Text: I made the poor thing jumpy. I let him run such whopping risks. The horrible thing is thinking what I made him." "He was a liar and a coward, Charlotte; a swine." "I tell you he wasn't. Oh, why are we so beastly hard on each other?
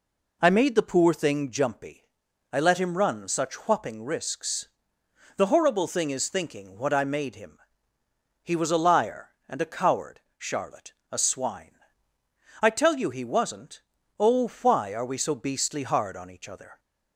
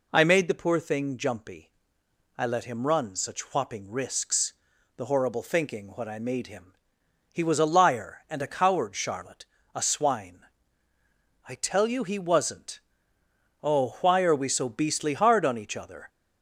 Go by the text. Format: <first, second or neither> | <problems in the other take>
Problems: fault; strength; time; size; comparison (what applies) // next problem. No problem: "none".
first | skips "thing is"; at 5.4 s